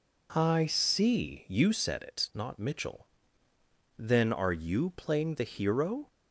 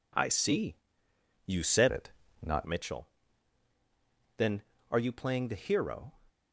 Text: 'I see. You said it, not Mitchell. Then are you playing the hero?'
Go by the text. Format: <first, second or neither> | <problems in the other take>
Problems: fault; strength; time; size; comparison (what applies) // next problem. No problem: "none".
first | changes voice from "it" to "not"; from 1.8 to 2.6 s; 0.8 s long